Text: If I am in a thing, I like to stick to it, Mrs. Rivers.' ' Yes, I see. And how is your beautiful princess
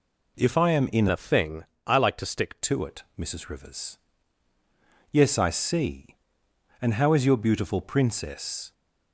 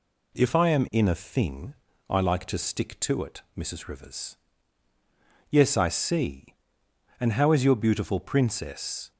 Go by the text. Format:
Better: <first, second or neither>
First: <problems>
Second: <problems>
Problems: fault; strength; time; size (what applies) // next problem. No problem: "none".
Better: second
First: changes voice from "a" to "stick"; from 1.0 to 2.6 s; 1.6 s long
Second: none